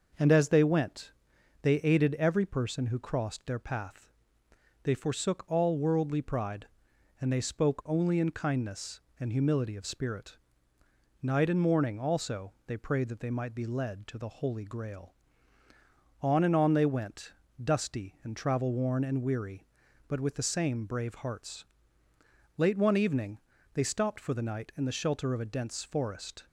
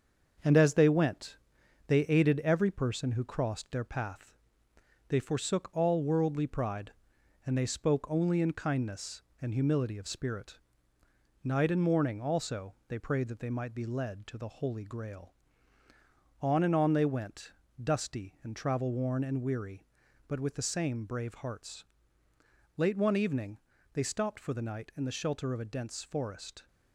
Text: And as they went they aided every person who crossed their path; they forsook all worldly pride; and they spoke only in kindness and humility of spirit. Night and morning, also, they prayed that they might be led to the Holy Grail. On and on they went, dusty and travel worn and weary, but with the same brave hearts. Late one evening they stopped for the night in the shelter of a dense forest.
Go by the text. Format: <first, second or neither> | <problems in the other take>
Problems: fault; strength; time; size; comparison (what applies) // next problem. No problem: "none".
first | gets quieter; noticeable; throughout; 5 dB // starts louder than the rest; until 1.9 s; 6.5 dB; noticeable in the first // pauses between "went" and "they"; noticeable; at 1.3 s; 0.50 s long; noticeable in the first // pauses between "evening" and "they"; at 23.5 s; 0.38 s long; also in the first